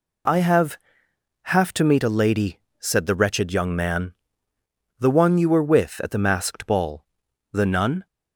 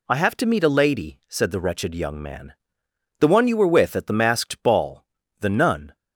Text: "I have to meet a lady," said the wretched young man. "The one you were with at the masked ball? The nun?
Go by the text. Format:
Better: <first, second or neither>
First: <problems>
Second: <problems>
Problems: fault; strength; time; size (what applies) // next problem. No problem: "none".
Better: second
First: says "have" twice; at 1.4 s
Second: none